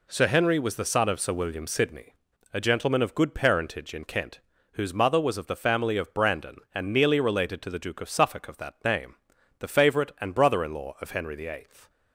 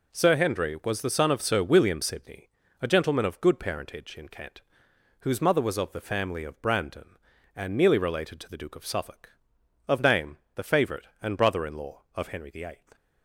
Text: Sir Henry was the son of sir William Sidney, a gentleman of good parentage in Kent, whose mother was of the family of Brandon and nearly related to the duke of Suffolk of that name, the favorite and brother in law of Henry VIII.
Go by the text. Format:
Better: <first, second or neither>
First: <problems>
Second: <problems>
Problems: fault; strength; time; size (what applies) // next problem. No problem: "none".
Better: first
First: none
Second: skips "that"; at 10.0 s